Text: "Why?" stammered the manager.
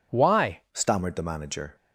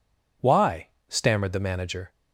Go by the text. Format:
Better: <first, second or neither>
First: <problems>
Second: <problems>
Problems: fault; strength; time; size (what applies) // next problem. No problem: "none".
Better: second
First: changes voice at "stammered"; from 0.7 s on; 1.0 s long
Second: none